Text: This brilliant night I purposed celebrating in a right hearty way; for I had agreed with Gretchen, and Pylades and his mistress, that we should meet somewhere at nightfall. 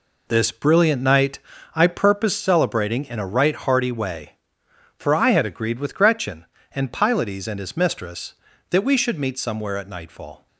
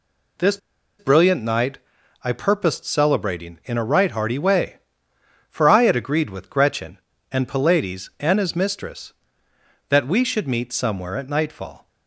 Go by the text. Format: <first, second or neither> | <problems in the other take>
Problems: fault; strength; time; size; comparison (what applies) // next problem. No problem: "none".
first | pauses between "This" and "brilliant"; at 0.5 s; 0.41 s long // pauses between "night" and "I"; at 1.7 s; 0.44 s long; slight in the first